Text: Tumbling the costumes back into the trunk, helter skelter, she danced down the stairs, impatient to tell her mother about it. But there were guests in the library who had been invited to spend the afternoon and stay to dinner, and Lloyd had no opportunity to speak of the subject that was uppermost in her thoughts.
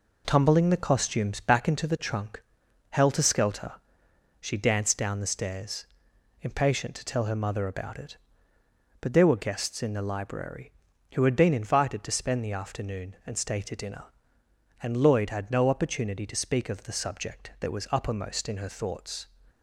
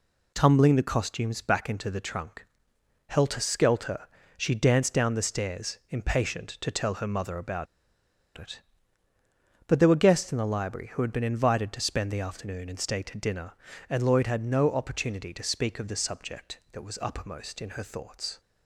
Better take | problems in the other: first | pauses between "about" and "it"; noticeable; at 7.6 s; 0.71 s long

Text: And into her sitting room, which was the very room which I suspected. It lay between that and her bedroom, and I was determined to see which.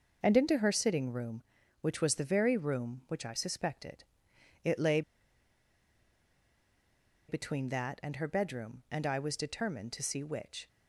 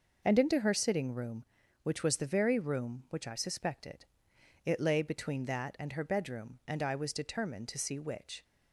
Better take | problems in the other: second | pauses between "lay" and "between"; strong; at 5.0 s; 2.2 s long

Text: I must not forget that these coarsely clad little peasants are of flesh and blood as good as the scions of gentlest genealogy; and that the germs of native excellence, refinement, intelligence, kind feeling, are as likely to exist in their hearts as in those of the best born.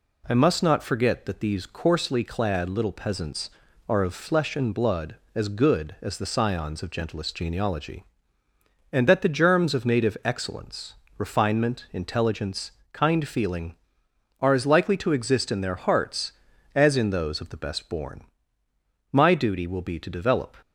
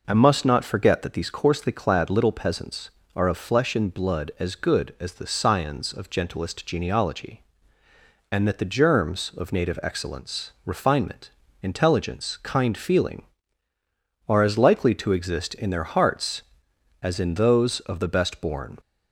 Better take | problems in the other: second | goes on to say "My duty will be to develop"; from 19.1 s on; 1.4 s long

